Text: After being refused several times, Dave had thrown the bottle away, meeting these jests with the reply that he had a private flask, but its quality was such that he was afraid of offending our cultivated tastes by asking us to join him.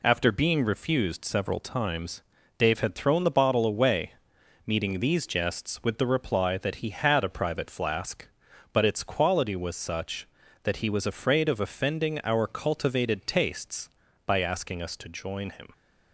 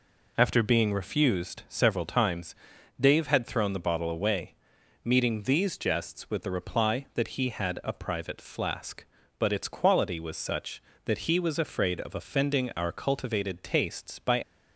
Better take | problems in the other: first | stops before "asking us to join him"; at 14.4 s

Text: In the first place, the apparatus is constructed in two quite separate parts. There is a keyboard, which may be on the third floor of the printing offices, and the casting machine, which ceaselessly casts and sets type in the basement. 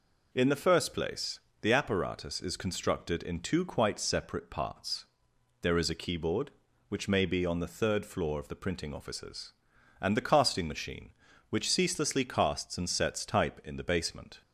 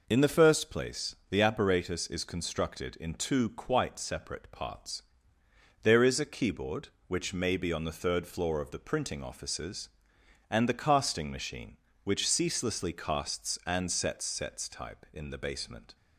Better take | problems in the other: first | says "sets" twice; at 14.2 s

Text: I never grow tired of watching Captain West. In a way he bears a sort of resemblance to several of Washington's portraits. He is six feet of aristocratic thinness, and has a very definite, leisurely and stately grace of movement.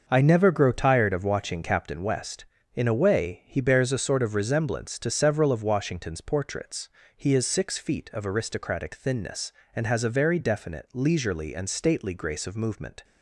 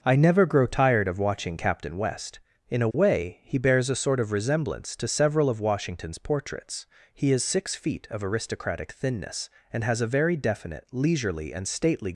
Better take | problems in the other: first | starts louder than the rest; until 1.0 s; 6 dB; also in the first // stops before "grace of movement"; at 12.1 s

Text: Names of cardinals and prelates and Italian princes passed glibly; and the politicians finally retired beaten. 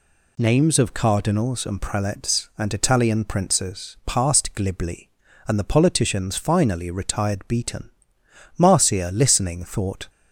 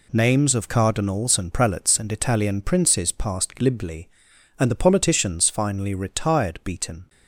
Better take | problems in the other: second | goes on to say "Marcia listening thought"; from 8.5 s on; 1.5 s long

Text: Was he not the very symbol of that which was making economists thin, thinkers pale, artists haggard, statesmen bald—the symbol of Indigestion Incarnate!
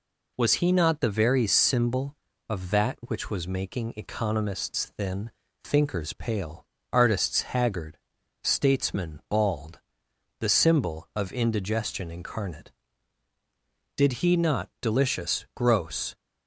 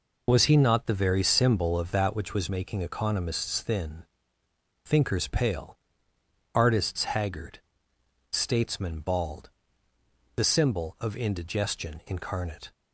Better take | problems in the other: second | goes on to say "Did he not delicious gross"; strong; from 13.9 s on; 2.2 s long

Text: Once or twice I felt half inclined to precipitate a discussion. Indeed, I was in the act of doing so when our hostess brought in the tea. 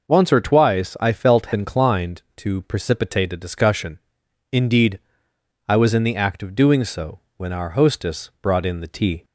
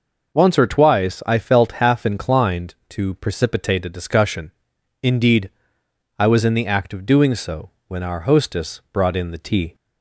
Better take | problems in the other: second | skips "half"; at 1.5 s // pauses between "so" and "when"; slight; at 7.2 s; 0.18 s long; slight in the second

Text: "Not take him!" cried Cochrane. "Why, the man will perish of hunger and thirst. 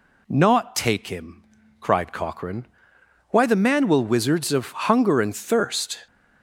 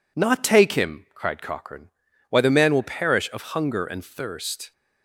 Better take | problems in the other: second | says "wizards" for "perish"; at 4.0 s

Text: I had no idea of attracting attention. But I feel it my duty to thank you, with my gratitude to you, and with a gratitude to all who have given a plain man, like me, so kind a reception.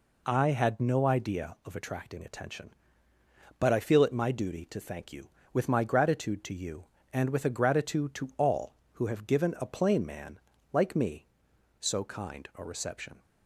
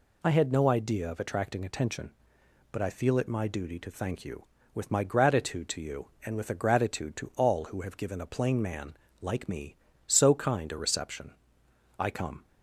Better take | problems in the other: first | goes on to say "I come"; slight; from 11.9 s on; 0.48 s long

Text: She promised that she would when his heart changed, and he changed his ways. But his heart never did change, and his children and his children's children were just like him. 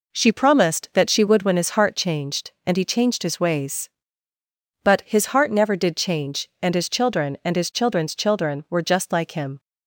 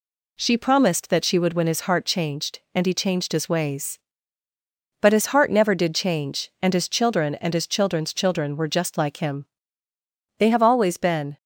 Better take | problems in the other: first | goes on to say "They have always been"; noticeable; from 10.3 s on; 1.0 s long

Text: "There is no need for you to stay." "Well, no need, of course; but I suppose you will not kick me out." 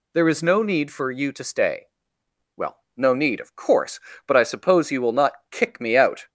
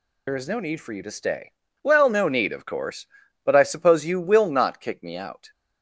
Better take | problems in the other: first | loses the start of "There"; at 0.2 s; 65 ms

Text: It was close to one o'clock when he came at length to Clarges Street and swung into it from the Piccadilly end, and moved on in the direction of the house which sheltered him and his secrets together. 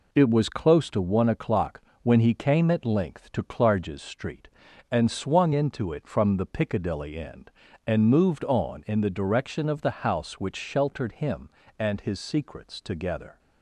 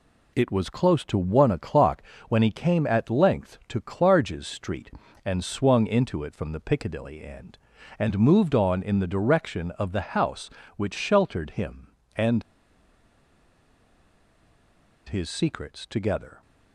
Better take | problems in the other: first | pauses between "o'clock" and "when"; slight; at 2.0 s; 0.28 s long; slight in the first // pauses between "and" and "his"; strong; at 12.4 s; 2.6 s long

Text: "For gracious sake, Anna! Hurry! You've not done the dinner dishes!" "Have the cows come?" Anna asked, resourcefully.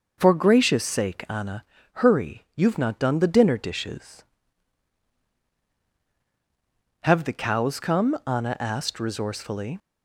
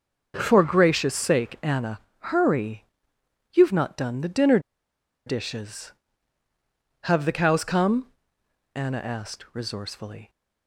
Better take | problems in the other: first | starts louder than the rest; noticeable; until 1.3 s; 6 dB // pauses between "dinner" and "dishes"; noticeable; at 4.5 s; 0.67 s long

